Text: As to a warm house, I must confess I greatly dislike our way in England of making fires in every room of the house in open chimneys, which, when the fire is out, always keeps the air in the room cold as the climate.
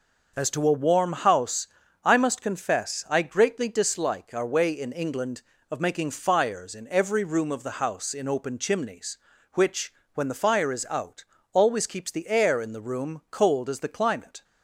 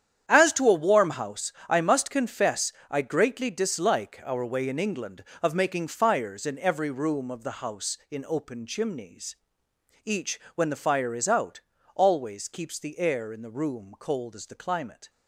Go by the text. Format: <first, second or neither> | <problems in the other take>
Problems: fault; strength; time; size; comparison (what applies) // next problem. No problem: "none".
first | starts louder than the rest; strong; until 1.3 s; 9.5 dB // pauses between "confess" and "I"; slight; at 2.7 s; 0.18 s long // says "each" for "which"; at 10.0 s